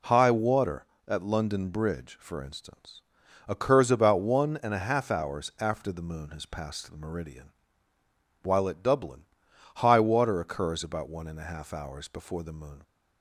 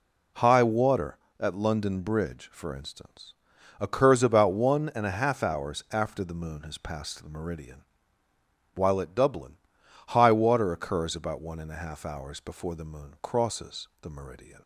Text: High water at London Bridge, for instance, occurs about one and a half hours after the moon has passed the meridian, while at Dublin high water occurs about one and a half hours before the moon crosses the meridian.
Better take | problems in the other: second | pauses between "Dublin" and "high"; noticeable; at 9.2 s; 0.52 s long; noticeable in the second // stops before "crosses the meridian"; at 12.8 s

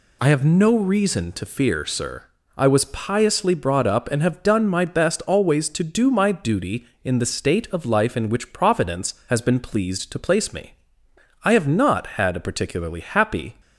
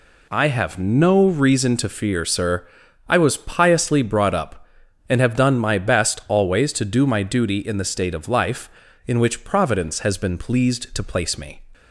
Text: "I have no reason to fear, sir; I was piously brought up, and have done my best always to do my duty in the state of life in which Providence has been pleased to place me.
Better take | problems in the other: second | goes on to say "I have not had a particularly happy"; strong; from 11.4 s on; 2.1 s long

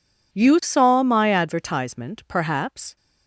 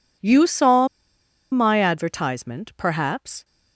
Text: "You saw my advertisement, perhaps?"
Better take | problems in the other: first | pauses between "saw" and "my"; noticeable; at 0.8 s; 0.65 s long

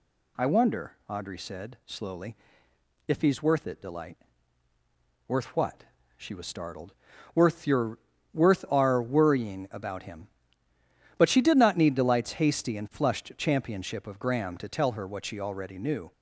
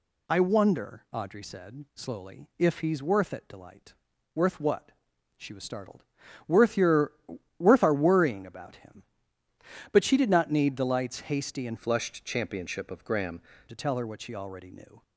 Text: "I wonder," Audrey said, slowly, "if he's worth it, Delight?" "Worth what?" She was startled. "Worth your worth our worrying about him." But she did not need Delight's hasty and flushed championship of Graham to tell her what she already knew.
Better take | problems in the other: first | pauses between "your" and "worth"; noticeable; at 7.1 s; 0.46 s long; slight in the first // changes voice from "flushed" to "Graham"; from 11.7 to 13.4 s; 1.7 s long

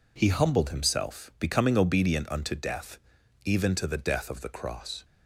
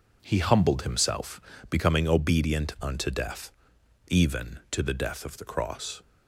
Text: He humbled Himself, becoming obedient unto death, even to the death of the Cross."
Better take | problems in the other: neither | none

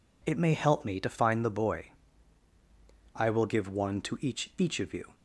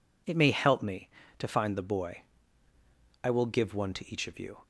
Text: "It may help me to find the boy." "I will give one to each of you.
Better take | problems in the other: second | says "each" twice; at 4.5 s

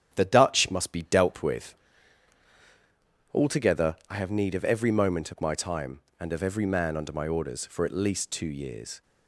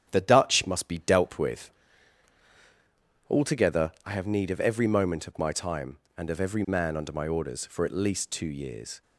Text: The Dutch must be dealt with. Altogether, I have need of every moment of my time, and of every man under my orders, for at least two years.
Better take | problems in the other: neither | starts louder than the rest; strong; the same in both

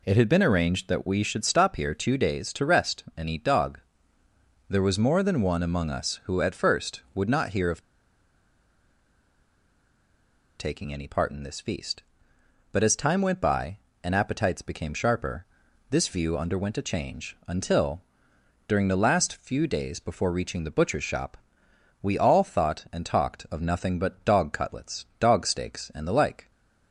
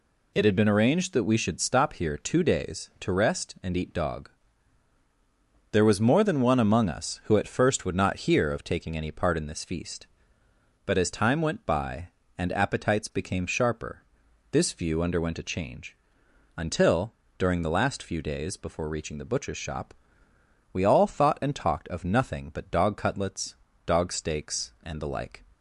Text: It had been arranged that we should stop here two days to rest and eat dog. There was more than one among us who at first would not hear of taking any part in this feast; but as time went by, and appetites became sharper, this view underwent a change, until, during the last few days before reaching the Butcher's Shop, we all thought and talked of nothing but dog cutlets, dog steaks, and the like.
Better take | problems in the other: second | pauses between "of" and "taking"; strong; at 7.7 s; 2.7 s long

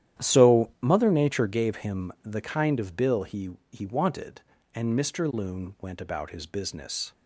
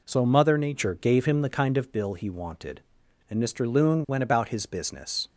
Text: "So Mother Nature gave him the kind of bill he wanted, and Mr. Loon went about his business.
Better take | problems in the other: second | starts louder than the rest; strong; until 1.2 s; 11 dB // says "he" twice; at 3.7 s

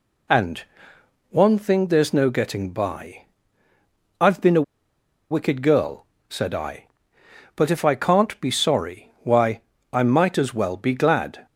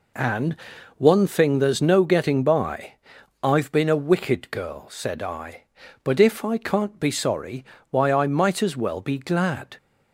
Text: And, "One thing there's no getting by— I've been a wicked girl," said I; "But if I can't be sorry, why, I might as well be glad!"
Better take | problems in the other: second | pauses between "a" and "wicked"; noticeable; at 4.6 s; 0.68 s long

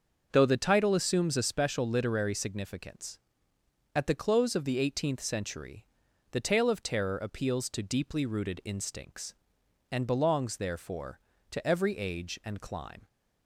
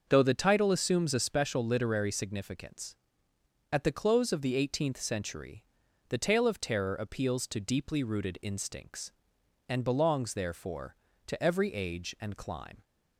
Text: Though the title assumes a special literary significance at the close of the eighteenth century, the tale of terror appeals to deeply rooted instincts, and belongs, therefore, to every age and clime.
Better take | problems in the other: neither | starts louder than the rest; the same in both

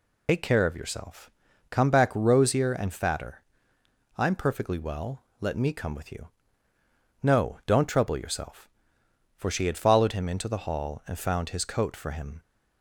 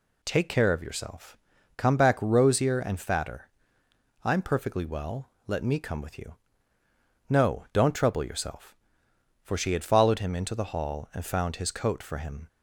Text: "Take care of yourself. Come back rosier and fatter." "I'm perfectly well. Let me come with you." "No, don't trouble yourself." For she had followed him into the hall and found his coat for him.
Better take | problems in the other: second | loses the start of "Take"; at 0.2 s; 115 ms

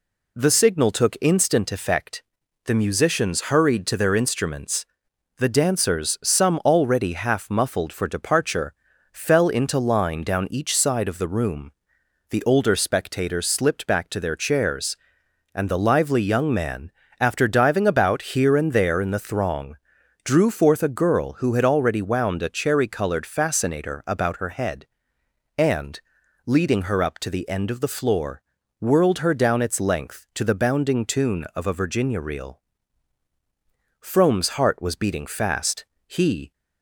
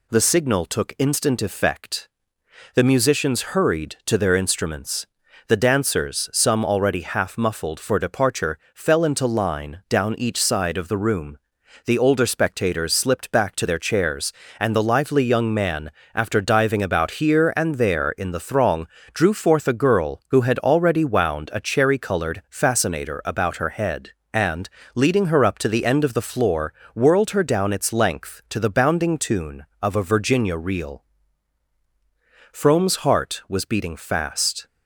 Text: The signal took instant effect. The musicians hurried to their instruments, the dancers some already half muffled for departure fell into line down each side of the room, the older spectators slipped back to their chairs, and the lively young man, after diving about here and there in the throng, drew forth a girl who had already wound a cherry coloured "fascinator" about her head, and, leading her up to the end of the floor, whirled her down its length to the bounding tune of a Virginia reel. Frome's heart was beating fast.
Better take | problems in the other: second | pauses between "departure" and "fell"; at 8.7 s; 0.40 s long; slight in the second // goes on to say "He"; slight; from 36.0 s on; 0.46 s long

